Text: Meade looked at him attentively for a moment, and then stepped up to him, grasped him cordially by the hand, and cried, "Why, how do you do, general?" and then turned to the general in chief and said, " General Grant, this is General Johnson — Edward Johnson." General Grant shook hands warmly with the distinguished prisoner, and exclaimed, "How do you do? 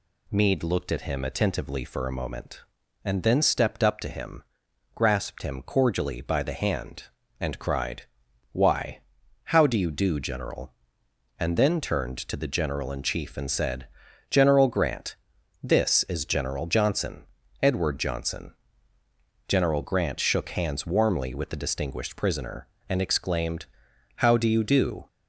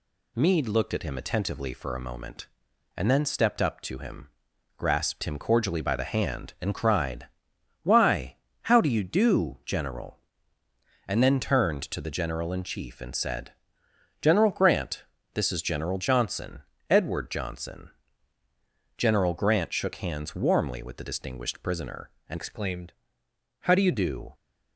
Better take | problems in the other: first | changes voice from "exclaimed" to "you"; from 22.3 to 23.9 s; 1.6 s long

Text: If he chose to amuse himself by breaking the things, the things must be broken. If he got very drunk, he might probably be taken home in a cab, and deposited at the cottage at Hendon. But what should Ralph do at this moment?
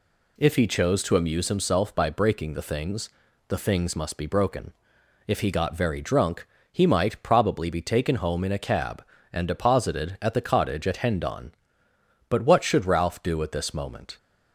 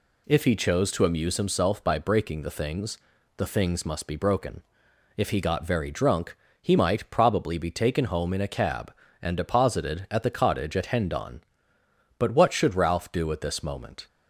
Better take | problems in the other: neither | none

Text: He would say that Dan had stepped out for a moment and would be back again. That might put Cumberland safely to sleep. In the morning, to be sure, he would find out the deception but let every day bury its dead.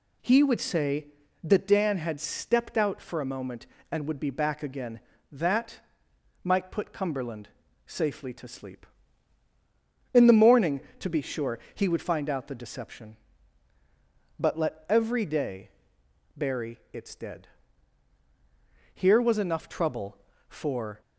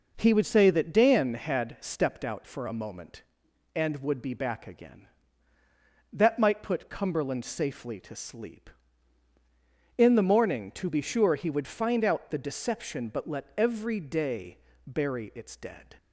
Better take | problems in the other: second | pauses between "That" and "might"; noticeable; at 5.7 s; 0.64 s long // pauses between "Cumberland" and "safely"; at 7.4 s; 0.38 s long // pauses between "day" and "bury"; noticeable; at 15.6 s; 0.66 s long; slight in the second // pauses between "bury" and "its"; slight; at 16.7 s; 0.16 s long // goes on to say "Here was enough trouble for"; strong; from 18.9 s on; 2.0 s long

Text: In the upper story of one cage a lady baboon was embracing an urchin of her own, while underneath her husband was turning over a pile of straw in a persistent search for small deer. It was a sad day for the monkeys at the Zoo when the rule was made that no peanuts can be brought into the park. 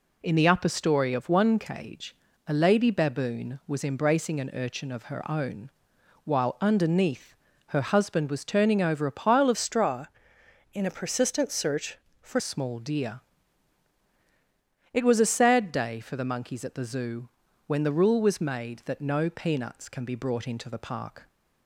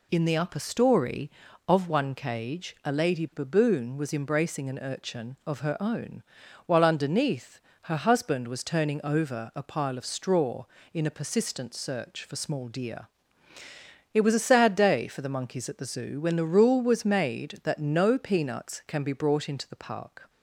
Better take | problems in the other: second | pauses between "cage" and "a"; slight; at 2.1 s; 0.32 s long // pauses between "underneath" and "her"; slight; at 7.3 s; 0.34 s long; slight in the second // changes voice from "straw" to "for"; from 9.5 to 12.3 s; 2.8 s long // pauses between "Zoo" and "when"; at 17.2 s; 0.38 s long

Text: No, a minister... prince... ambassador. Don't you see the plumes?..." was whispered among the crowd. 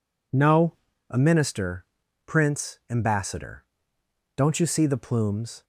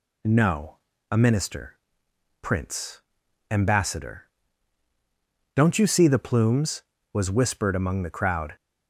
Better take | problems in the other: second | stops before "was whispered among the crowd"; at 5.6 s

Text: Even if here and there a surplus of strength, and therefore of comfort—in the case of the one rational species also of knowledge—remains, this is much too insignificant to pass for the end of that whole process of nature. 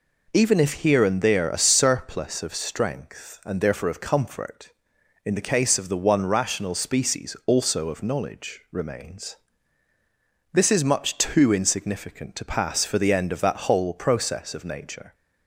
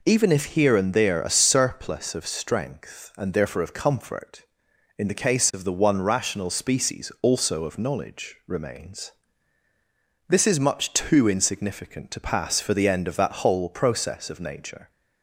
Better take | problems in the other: neither | none

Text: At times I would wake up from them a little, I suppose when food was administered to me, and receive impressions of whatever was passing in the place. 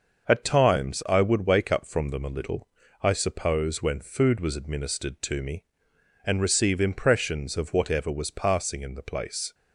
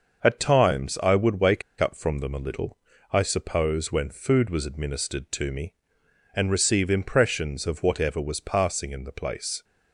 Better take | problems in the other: first | starts louder than the rest; until 1.2 s; 6 dB; also in the first // pauses between "wake" and "up"; slight; at 1.6 s; 0.17 s long

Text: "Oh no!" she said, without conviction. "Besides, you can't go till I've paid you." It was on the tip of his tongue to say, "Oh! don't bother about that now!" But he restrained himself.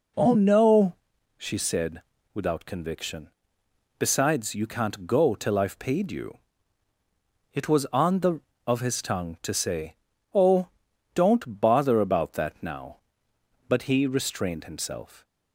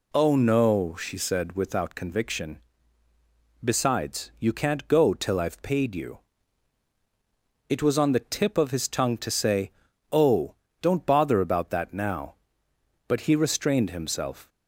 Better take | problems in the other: second | skips "tip"; at 8.5 s

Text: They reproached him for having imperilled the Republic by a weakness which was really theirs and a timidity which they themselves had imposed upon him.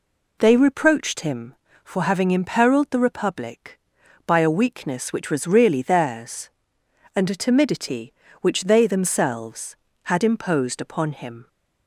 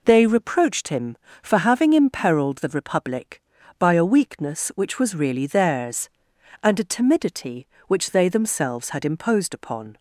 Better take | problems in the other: first | stops before "him"; at 9.9 s

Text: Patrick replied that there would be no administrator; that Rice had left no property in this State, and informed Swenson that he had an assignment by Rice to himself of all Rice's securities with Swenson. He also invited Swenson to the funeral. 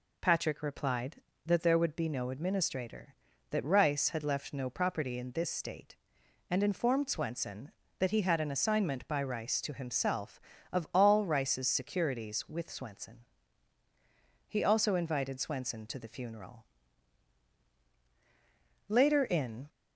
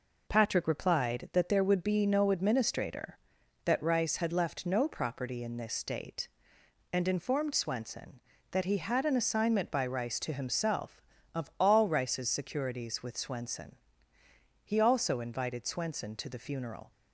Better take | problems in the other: second | goes on to say "Later in"; noticeable; from 18.8 s on; 0.80 s long

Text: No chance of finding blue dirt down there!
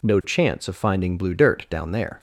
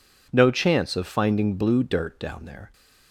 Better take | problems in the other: neither | none

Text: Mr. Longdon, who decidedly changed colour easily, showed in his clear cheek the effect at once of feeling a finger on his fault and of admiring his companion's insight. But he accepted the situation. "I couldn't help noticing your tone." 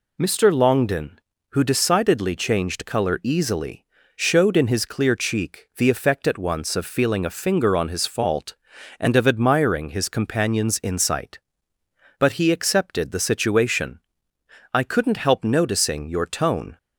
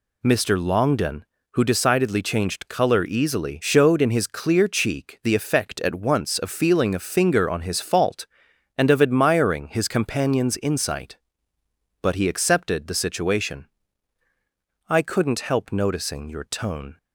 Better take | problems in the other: neither | none

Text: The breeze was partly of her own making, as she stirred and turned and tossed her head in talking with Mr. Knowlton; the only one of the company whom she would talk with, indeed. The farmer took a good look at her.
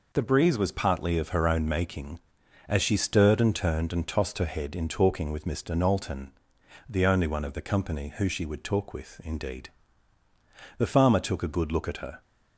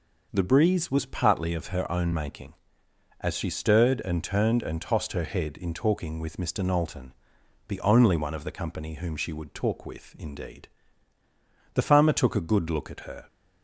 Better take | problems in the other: second | says "who" for "whom"; at 8.1 s

